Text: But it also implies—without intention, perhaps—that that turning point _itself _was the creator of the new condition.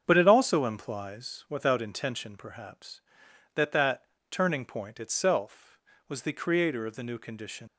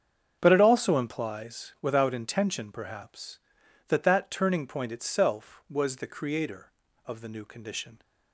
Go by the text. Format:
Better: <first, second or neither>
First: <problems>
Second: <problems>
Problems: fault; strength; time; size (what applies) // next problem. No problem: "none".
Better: second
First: starts louder than the rest; strong; until 1.0 s; 7.5 dB // pauses between "that" and "turning"; slight; at 4.0 s; 0.26 s long // leaves "condition" unfinished; at 7.6 s; 80 ms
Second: starts louder than the rest; strong; until 1.4 s; 7.5 dB